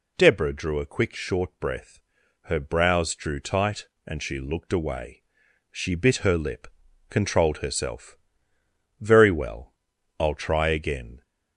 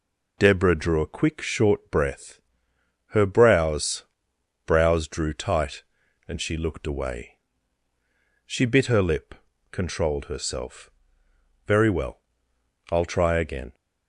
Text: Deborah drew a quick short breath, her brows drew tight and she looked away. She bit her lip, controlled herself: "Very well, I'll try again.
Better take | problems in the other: first | says "brows" twice; at 4.6 s

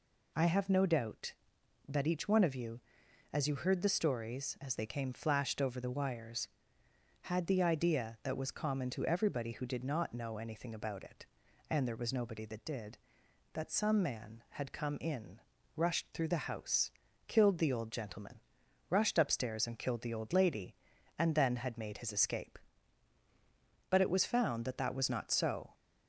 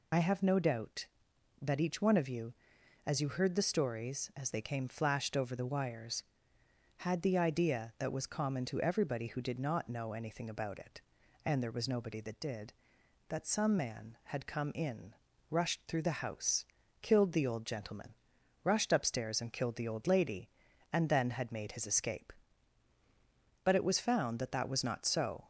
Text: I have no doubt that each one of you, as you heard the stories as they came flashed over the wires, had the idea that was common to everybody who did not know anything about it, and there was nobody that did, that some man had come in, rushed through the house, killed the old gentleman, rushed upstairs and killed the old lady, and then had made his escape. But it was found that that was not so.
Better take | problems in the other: first | loses the start of "I"; at 0.1 s; 40 ms

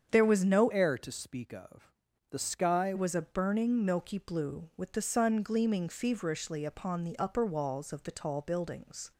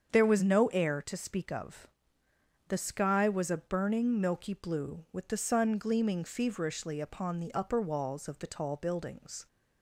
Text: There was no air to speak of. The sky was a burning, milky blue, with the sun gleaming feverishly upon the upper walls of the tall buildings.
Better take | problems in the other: second | starts louder than the rest; strong; until 1.1 s; 7.5 dB; strong in the second // changes voice from "air" to "sky"; from 0.7 to 2.9 s; 2.2 s long

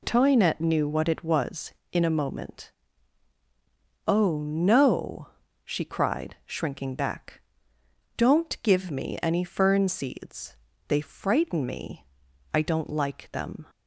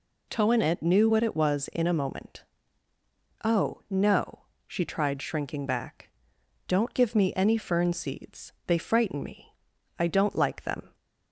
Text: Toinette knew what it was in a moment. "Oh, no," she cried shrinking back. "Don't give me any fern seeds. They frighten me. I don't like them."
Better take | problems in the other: first | says "tried" for "cried"; at 4.8 s

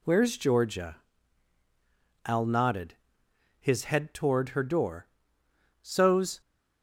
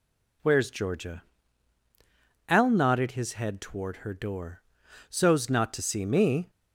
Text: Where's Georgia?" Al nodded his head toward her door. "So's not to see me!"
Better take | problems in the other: second | pauses between "nodded" and "his"; noticeable; at 2.9 s; 0.64 s long // stops before "not to see me"; at 6.4 s

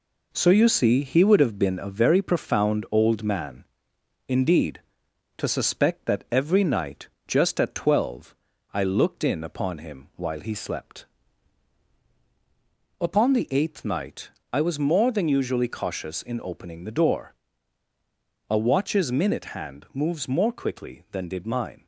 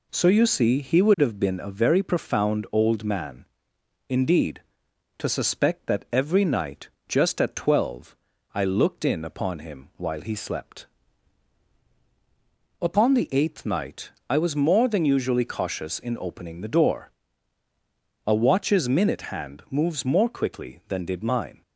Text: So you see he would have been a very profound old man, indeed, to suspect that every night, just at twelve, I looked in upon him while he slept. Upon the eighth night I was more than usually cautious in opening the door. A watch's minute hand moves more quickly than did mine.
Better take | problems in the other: second | gets quieter; noticeable; throughout; 4.5 dB // pauses between "night" and "I"; slight; at 14.2 s; 0.22 s long; slight in the second

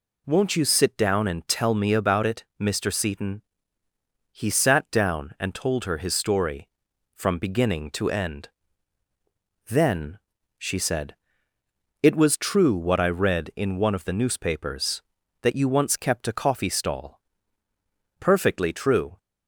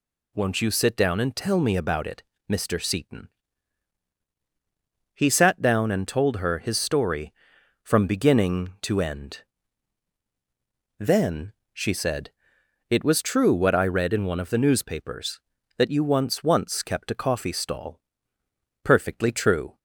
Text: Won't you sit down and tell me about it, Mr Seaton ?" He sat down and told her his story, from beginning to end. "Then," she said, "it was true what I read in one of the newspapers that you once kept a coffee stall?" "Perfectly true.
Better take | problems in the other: first | says "once" twice; at 16.4 s

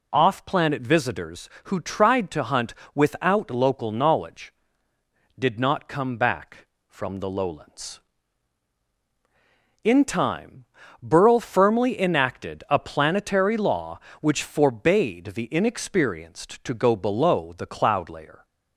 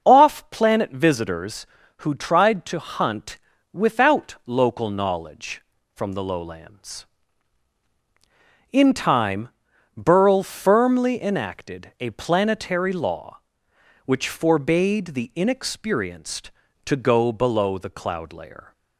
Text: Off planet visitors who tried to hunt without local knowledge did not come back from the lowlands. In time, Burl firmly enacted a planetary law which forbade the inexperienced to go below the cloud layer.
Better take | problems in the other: first | starts louder than the rest; until 1.0 s; 6 dB // pauses between "hunt" and "without"; slight; at 3.3 s; 0.34 s long; slight in the first // skips "did not come back"; at 5.7 s

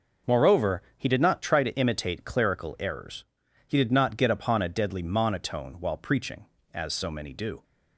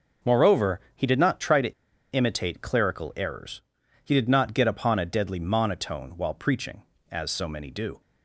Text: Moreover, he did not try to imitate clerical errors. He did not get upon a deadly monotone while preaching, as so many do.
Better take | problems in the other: first | pauses between "to" and "imitate"; at 1.7 s; 0.38 s long

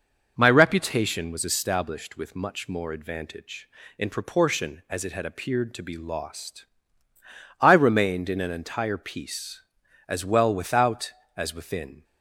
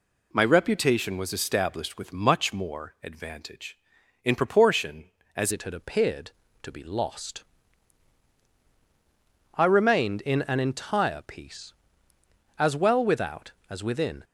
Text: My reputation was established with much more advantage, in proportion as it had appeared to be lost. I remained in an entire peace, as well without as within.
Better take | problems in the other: first | changes voice at "it"; from 5.5 s on; 8.7 s long

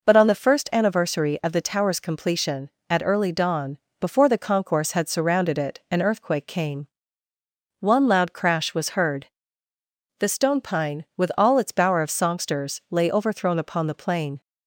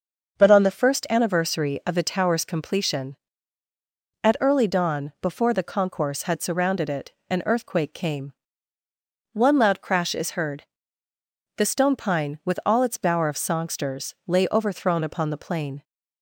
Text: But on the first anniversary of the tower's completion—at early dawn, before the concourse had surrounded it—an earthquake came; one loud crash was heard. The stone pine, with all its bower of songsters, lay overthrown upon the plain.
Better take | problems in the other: first | starts louder than the rest; until 1.4 s; 6.5 dB // says "is" for "was"; at 10.1 s

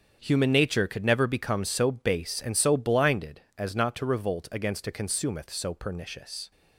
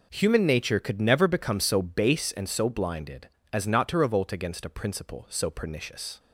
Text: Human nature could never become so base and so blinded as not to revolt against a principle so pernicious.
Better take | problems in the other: second | starts louder than the rest; strong; until 1.2 s; 7.5 dB // says "consumeth" for "principle"; at 4.9 s

